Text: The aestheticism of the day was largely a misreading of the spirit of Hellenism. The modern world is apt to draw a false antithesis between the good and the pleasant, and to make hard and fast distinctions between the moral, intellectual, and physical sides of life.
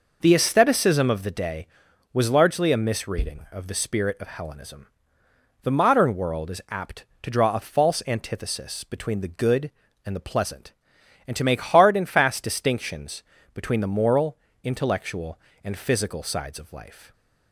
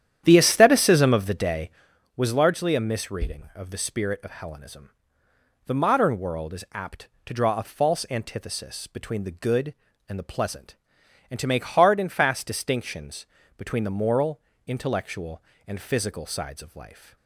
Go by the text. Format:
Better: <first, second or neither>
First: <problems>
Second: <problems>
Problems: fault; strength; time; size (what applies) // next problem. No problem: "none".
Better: first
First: pauses between "distinctions" and "between"; slight; at 13.2 s; 0.30 s long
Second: starts louder than the rest; strong; until 1.9 s; 10 dB // pauses between "distinctions" and "between"; slight; at 13.2 s; 0.30 s long